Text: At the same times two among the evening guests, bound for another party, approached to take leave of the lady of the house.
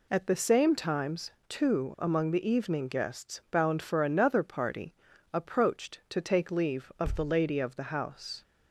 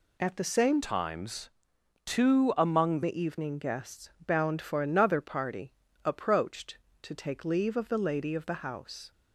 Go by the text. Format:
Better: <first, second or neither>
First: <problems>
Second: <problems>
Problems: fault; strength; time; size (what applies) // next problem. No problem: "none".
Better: first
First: pauses between "times" and "two"; slight; at 1.3 s; 0.18 s long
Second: changes voice from "times" to "among"; from 0.8 to 3.0 s; 2.2 s long // pauses between "times" and "two"; noticeable; at 1.4 s; 0.56 s long